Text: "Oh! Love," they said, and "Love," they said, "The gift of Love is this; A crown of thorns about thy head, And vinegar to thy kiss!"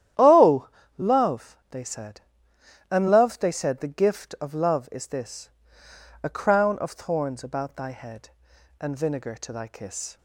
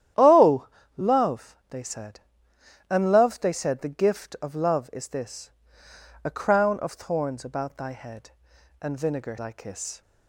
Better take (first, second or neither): first